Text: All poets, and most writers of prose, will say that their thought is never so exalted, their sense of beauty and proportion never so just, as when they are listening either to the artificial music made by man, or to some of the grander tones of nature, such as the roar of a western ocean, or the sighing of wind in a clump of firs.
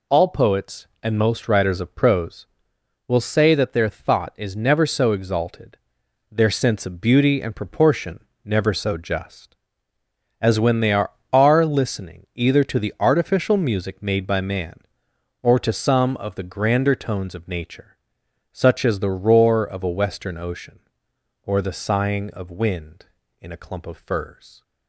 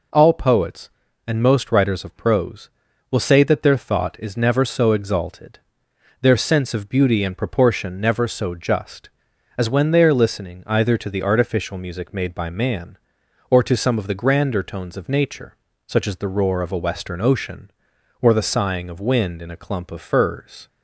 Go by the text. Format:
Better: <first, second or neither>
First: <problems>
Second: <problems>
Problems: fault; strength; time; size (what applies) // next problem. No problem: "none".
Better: second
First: pauses between "proportion" and "never"; slight; at 8.2 s; 0.18 s long // says "are" twice; at 11.3 s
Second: none